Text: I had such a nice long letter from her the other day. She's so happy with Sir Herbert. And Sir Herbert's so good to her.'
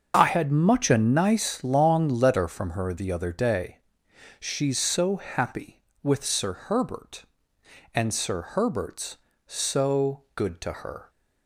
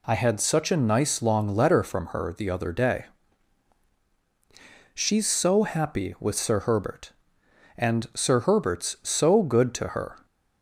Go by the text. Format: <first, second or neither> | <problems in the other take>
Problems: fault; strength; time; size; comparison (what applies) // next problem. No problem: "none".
second | starts louder than the rest; until 1.1 s; 6.5 dB // says "much" for "such"; at 0.4 s